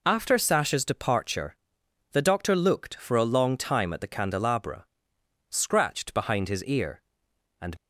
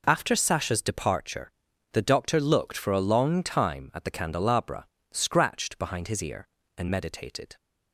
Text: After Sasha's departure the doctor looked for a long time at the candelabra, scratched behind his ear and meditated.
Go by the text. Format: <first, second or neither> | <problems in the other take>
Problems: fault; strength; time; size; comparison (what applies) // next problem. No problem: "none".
second | pauses between "departure" and "the"; noticeable; at 1.5 s; 0.56 s long; also in the second // stops before "meditated"; at 7.7 s